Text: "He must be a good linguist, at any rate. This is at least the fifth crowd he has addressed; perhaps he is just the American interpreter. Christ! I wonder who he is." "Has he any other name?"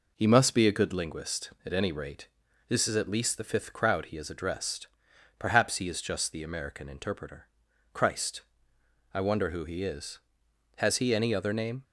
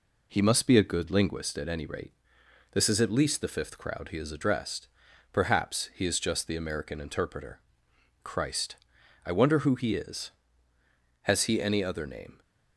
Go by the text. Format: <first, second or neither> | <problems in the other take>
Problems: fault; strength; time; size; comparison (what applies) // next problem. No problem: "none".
neither | none